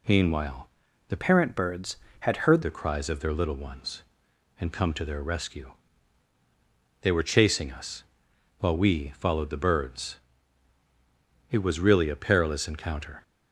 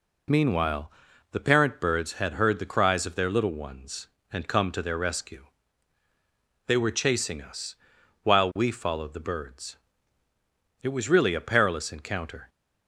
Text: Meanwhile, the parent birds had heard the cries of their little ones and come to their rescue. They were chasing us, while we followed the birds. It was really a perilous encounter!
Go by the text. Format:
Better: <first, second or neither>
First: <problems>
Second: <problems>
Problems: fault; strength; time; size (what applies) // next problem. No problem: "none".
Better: second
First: changes voice from "parent" to "heard"; from 1.1 to 2.6 s; 1.5 s long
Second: none